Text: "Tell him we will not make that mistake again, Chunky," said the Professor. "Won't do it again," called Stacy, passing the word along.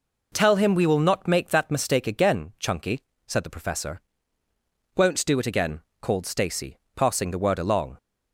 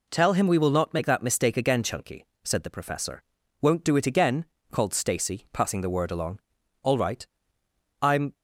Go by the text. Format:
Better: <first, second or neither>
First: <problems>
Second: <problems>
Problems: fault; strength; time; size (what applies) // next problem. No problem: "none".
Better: first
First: none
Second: goes on to say "All right I'm"; from 6.8 s on; 1.5 s long